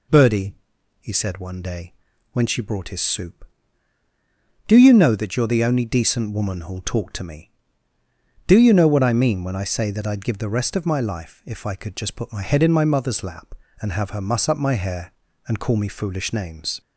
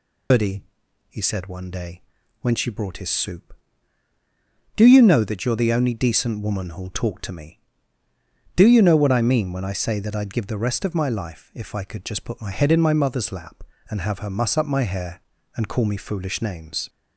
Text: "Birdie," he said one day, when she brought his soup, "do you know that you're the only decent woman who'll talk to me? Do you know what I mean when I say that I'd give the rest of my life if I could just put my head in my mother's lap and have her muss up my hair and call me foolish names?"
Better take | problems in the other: first | loses the start of "Birdie"; at 0.3 s; 115 ms

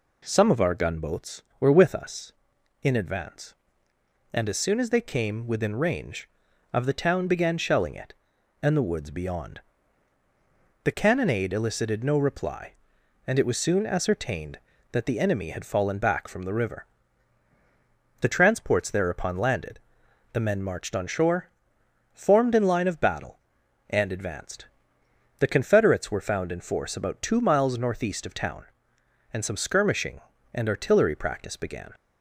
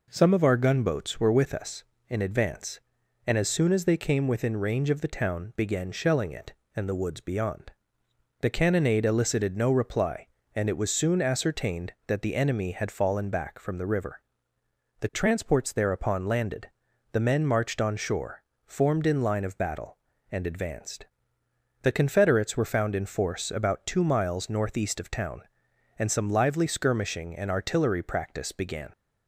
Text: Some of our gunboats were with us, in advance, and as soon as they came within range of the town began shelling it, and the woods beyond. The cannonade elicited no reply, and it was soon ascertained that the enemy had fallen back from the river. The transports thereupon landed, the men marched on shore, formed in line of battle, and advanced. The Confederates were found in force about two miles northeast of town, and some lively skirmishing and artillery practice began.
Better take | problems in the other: second | skips "lively"; at 29.5 s

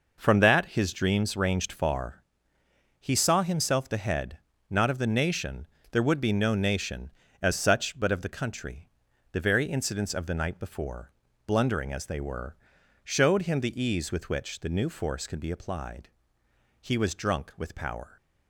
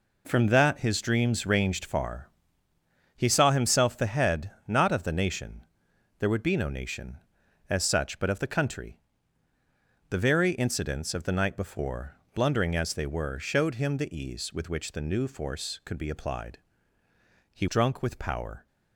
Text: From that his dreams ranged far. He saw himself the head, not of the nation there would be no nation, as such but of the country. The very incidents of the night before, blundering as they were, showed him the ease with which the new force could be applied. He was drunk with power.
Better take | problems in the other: first | pauses between "nation" and "there"; noticeable; at 5.6 s; 0.56 s long; slight in the first // skips "was"; at 17.6 s

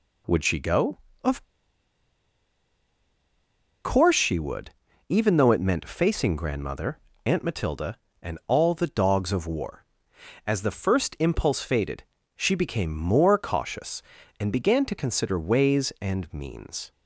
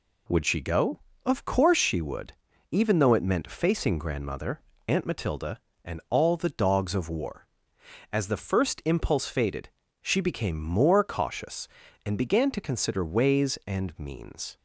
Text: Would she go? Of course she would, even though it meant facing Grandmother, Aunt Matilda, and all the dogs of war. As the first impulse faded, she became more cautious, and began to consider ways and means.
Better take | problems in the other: second | pauses between "Of" and "course"; strong; at 1.4 s; 2.4 s long

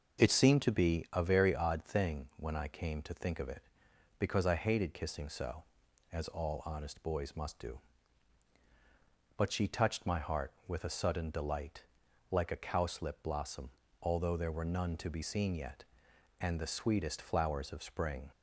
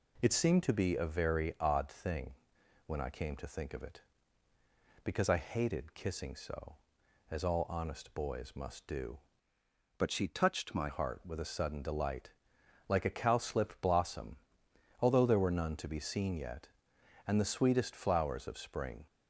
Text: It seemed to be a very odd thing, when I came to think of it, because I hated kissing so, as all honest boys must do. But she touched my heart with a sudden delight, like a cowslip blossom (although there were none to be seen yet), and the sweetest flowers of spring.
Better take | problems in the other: first | changes voice from "But" to "my"; from 9.9 to 10.8 s; 0.9 s long

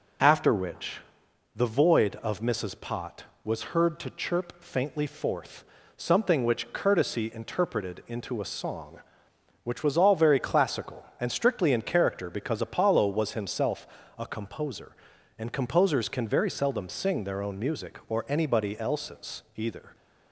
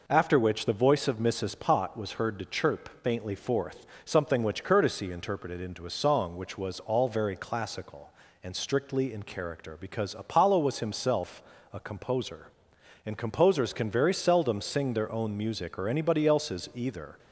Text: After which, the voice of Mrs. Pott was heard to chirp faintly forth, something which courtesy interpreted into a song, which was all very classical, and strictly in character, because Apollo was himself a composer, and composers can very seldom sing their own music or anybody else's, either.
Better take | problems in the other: second | says "void" for "voice"; at 1.6 s // pauses between "himself" and "a"; slight; at 13.8 s; 0.32 s long; slight in the second

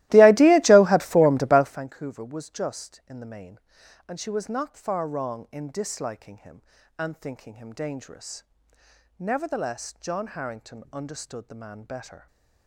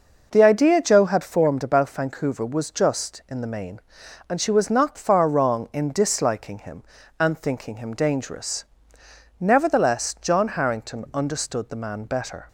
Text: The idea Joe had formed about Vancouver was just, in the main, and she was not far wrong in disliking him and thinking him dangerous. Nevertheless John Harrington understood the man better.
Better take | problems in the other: second | starts louder than the rest; strong; until 1.9 s; 17 dB

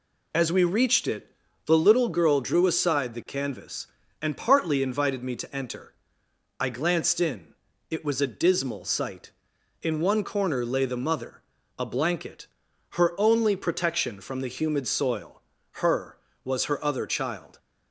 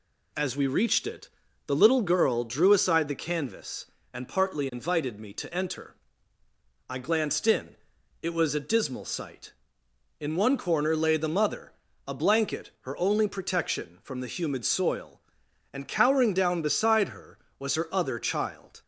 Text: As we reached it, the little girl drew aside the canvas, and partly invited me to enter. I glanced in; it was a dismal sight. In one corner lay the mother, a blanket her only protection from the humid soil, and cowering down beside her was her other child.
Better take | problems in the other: second | pauses between "blanket" and "her"; noticeable; at 12.4 s; 0.46 s long // skips "and cowering down beside"; at 15.6 s

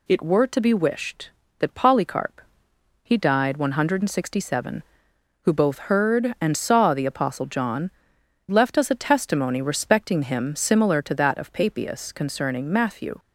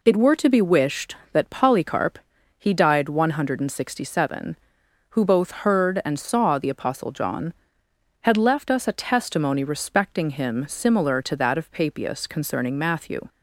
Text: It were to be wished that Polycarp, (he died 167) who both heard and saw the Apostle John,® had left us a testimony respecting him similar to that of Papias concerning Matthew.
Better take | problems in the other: second | skips "had"; at 8.2 s

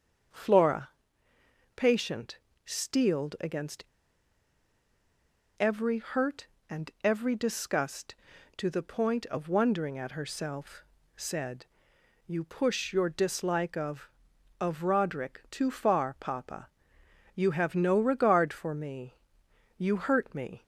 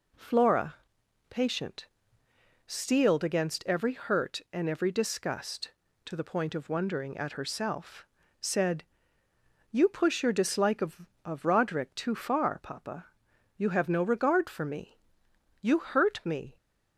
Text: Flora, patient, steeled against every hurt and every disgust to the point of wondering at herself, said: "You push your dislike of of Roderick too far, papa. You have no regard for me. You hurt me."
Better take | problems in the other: second | starts louder than the rest; until 2.1 s; 7 dB // pauses between "against" and "every"; strong; at 3.8 s; 1.7 s long

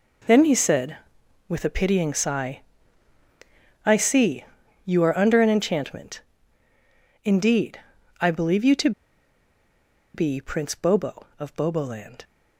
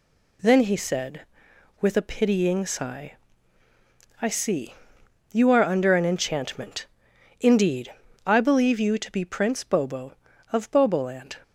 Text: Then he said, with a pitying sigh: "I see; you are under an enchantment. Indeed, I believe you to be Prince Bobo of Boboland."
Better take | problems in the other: second | pauses between "to" and "be"; at 8.9 s; 1.2 s long

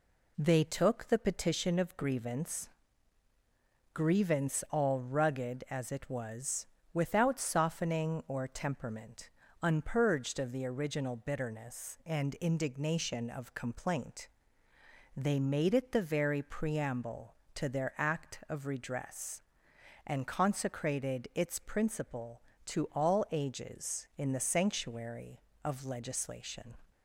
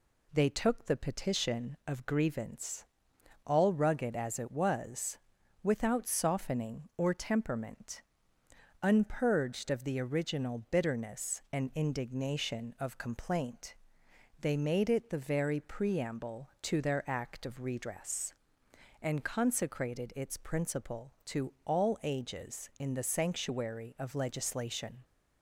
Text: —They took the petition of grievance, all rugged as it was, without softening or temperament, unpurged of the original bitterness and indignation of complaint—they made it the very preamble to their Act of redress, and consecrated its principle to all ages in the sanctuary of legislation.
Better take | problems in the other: second | says "grievance" twice; at 3.9 s

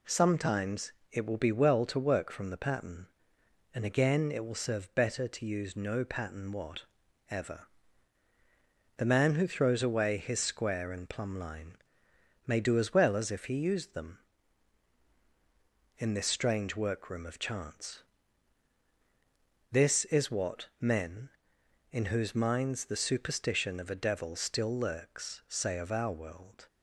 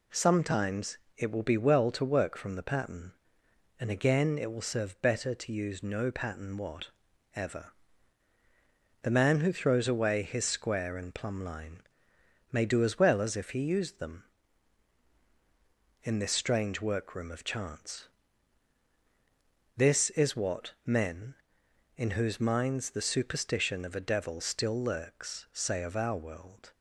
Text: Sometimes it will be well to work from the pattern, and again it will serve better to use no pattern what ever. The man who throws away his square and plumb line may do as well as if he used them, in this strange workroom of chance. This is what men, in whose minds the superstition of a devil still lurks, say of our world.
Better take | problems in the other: neither | pauses between "Sometimes" and "it"; slight; the same in both // pauses between "what" and "ever"; noticeable; the same in both // pauses between "line" and "may"; noticeable; the same in both

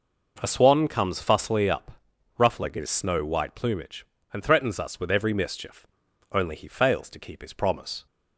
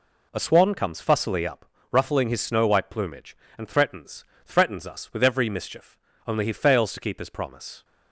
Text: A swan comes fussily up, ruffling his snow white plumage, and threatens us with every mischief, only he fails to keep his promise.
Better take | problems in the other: first | says "threatens" twice; at 4.4 s

